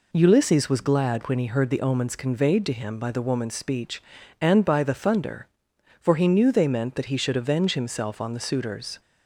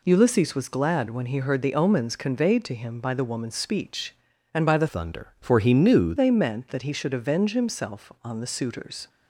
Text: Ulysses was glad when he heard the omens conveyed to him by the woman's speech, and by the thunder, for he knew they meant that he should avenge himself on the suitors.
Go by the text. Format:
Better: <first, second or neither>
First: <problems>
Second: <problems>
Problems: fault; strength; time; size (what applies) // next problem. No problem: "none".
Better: first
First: none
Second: changes voice from "thunder" to "knew"; from 4.8 to 6.1 s; 1.3 s long